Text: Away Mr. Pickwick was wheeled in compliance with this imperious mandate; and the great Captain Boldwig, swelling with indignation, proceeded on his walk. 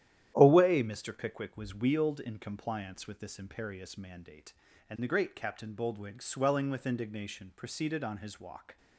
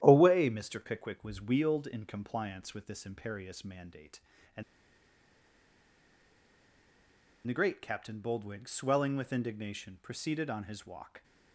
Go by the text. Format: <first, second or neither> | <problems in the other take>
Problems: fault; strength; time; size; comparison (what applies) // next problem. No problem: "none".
first | starts louder than the rest; strong; until 1.0 s; 11 dB; strong in the first // pauses between "and" and "the"; strong; at 4.6 s; 2.8 s long